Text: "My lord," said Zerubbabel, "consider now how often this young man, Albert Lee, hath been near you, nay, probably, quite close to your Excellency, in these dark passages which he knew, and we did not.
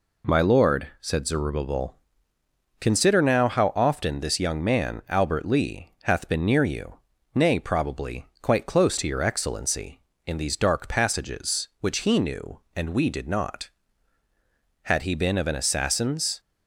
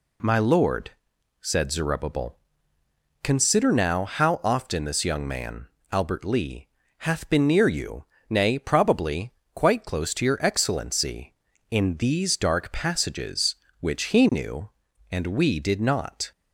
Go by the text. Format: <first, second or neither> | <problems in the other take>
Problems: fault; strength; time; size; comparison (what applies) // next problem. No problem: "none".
second | goes on to say "Had he been of an assassin's"; from 14.8 s on; 1.5 s long